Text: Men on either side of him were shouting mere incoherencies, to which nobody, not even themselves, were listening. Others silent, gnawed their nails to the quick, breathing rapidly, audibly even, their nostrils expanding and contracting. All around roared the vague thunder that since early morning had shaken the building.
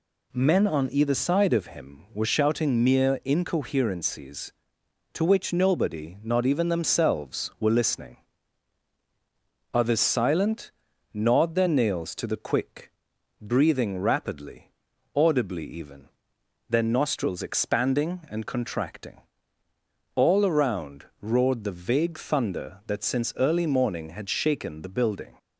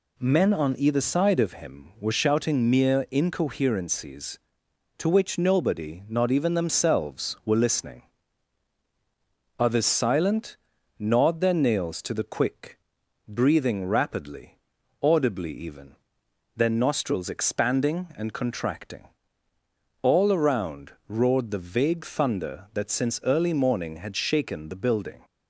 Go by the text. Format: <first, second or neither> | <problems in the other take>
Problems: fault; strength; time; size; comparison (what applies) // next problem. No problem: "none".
neither | pauses between "around" and "roared"; slight; the same in both